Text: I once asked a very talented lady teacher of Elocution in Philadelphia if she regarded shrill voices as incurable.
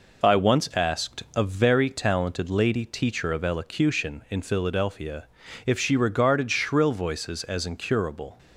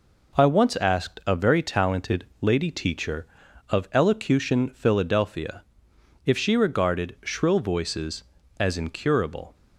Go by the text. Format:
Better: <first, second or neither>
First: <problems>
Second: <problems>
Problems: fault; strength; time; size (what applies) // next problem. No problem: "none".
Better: first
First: pauses between "Philadelphia" and "if"; at 5.2 s; 0.40 s long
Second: skips "in"; at 4.6 s // pauses between "Philadelphia" and "if"; noticeable; at 5.6 s; 0.64 s long